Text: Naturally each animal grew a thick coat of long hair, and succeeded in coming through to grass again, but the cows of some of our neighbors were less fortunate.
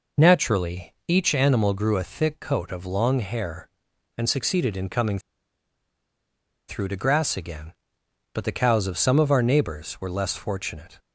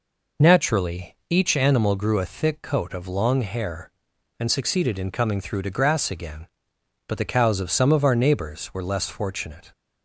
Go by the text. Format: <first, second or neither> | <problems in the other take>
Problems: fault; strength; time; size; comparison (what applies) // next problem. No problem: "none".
second | pauses between "coming" and "through"; strong; at 5.1 s; 1.4 s long